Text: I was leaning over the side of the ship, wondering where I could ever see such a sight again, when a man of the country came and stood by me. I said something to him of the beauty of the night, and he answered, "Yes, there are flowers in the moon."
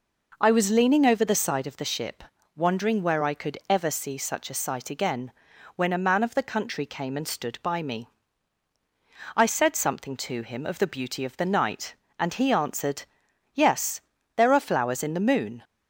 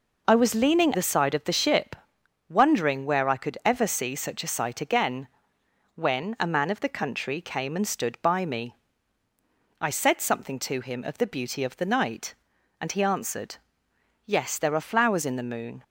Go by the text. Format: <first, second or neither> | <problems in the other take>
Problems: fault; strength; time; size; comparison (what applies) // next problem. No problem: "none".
first | skips "over"; at 0.9 s